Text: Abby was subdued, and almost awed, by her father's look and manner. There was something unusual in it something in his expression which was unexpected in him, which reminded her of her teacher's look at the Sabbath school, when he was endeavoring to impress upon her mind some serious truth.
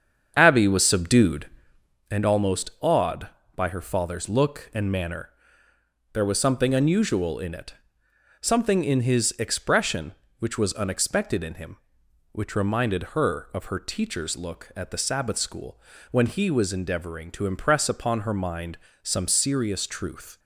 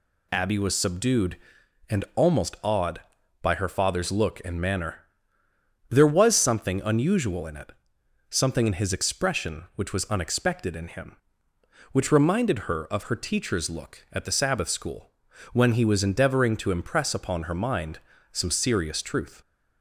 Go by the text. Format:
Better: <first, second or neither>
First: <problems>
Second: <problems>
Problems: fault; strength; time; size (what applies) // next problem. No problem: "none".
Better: second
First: starts louder than the rest; strong; until 2.0 s; 7.5 dB // pauses between "it" and "something"; noticeable; at 7.7 s; 0.66 s long // pauses between "mind" and "some"; slight; at 18.7 s; 0.24 s long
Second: pauses between "it" and "something"; noticeable; at 7.7 s; 0.58 s long // pauses between "mind" and "some"; slight; at 17.9 s; 0.32 s long